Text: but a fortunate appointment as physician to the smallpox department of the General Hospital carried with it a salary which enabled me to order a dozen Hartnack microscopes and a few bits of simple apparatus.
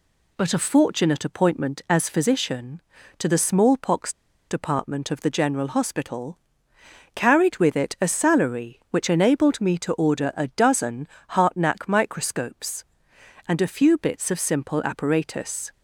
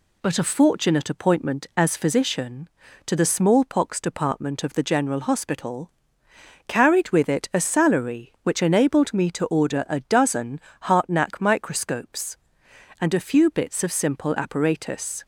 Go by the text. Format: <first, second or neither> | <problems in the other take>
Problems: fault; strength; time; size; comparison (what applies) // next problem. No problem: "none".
second | pauses between "smallpox" and "department"; at 4.1 s; 0.37 s long // pauses between "Hospital" and "carried"; noticeable; at 6.3 s; 0.78 s long; noticeable in the second // pauses between "dozen" and "Hartnack"; slight; at 11.0 s; 0.24 s long; slight in the second